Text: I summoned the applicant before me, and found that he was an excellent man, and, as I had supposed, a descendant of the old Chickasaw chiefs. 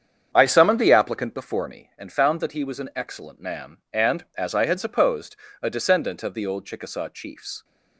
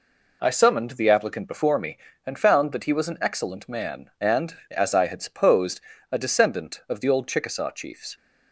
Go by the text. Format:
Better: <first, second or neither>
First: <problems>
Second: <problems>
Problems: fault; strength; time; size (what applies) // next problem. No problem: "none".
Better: second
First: starts louder than the rest; strong; until 1.8 s; 8 dB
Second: none